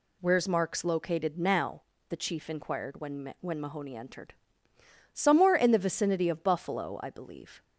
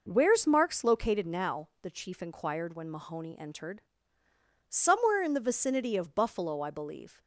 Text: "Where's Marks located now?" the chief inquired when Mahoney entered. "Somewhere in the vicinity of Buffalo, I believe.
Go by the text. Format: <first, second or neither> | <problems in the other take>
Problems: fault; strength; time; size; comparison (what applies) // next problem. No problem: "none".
second | says "when" twice; at 3.3 s